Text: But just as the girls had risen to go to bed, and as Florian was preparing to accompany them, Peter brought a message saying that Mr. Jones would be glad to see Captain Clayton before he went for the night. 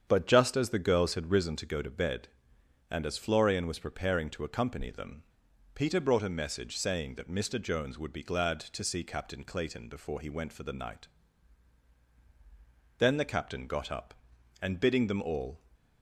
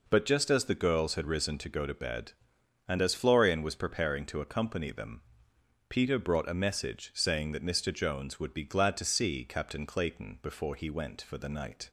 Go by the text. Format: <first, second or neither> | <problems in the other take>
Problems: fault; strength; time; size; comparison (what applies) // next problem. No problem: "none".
second | starts louder than the rest; strong; until 1.0 s; 8 dB // goes on to say "Then the Captain got up and bidding them all"; strong; from 12.9 s on; 2.6 s long